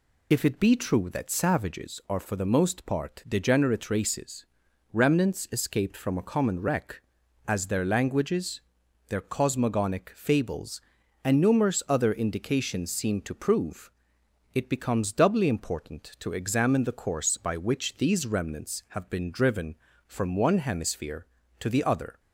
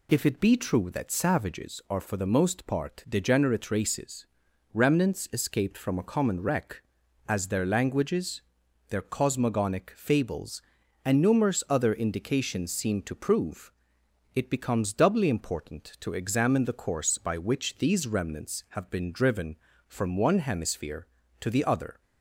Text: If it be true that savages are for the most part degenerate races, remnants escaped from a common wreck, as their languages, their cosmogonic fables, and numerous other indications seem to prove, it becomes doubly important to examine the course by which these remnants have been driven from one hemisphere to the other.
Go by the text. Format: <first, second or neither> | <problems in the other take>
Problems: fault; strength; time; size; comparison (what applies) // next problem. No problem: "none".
second | loses the start of "If"; at 0.3 s; 20 ms